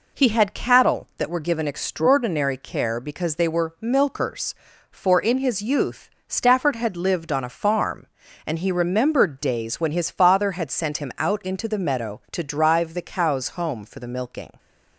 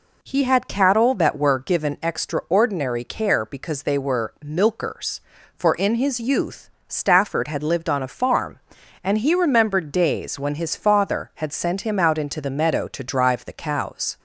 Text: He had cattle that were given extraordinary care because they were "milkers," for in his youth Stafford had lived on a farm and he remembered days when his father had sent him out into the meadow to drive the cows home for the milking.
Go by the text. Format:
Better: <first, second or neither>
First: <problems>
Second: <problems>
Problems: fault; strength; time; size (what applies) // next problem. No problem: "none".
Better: first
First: pauses between "youth" and "Stafford"; slight; at 6.0 s; 0.20 s long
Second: pauses between "youth" and "Stafford"; slight; at 6.6 s; 0.18 s long // stops before "home for the milking"; at 14.1 s